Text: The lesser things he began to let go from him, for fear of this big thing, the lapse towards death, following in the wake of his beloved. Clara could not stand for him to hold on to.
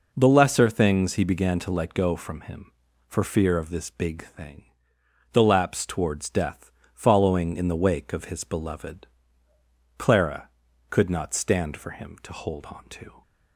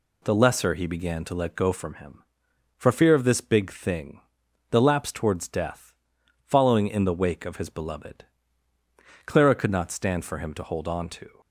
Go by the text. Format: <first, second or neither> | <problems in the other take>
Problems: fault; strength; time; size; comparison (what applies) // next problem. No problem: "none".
first | skips "things"; at 0.7 s